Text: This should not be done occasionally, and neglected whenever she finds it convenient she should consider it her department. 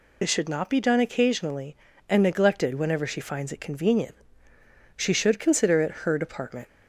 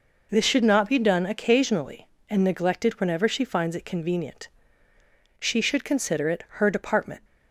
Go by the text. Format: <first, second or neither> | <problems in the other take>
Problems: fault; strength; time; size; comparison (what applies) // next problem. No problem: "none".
second | loses the start of "This"; at 0.2 s; 45 ms // pauses between "convenient" and "she"; noticeable; at 4.1 s; 0.80 s long; noticeable in the second